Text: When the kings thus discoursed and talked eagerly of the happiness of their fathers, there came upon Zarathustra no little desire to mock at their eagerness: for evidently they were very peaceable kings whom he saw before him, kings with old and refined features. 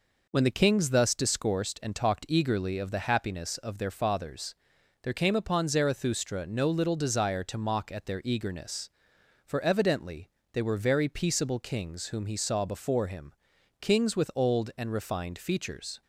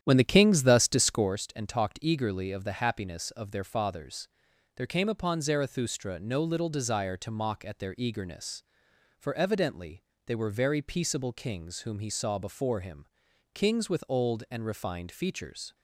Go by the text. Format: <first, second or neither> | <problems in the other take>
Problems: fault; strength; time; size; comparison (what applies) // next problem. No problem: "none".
first | starts louder than the rest; strong; until 1.3 s; 10 dB // pauses between "evidently" and "they"; slight; at 10.0 s; 0.22 s long; slight in the first